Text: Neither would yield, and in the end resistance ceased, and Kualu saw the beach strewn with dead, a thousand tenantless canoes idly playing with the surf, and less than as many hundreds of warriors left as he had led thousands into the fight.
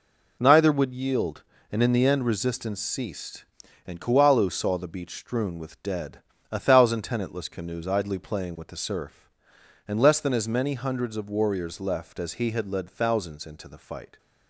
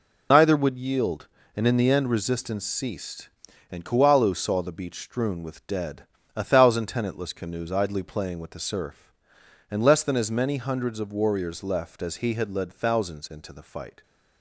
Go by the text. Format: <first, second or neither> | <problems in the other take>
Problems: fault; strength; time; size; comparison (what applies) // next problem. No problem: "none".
first | loses the start of "Neither"; at 0.3 s; 60 ms